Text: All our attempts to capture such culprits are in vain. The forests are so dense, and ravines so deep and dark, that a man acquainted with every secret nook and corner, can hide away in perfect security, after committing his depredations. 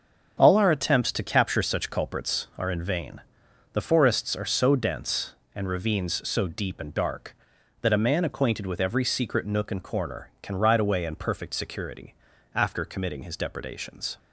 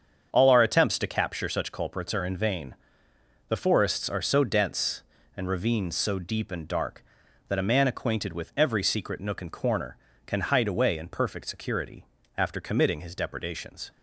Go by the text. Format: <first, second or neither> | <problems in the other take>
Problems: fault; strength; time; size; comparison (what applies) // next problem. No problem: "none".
second | starts louder than the rest; strong; until 1.4 s; 7.5 dB; strong in the second // says "ride" for "hide"; at 10.5 s